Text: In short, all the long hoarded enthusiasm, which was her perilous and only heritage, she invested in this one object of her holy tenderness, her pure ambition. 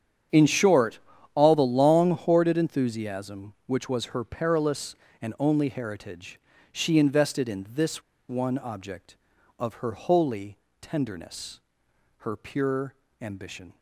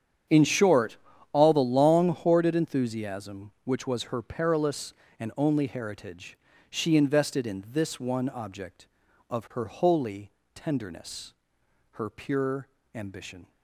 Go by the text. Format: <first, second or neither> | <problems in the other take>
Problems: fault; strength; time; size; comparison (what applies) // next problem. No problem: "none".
second | starts louder than the rest; strong; until 1.6 s; 8.5 dB; strong in the second // pauses between "this" and "one"; slight; at 8.0 s; 0.27 s long // pauses between "holy" and "tenderness"; slight; at 10.5 s; 0.22 s long; slight in the second // pauses between "pure" and "ambition"; slight; at 12.9 s; 0.28 s long; slight in the second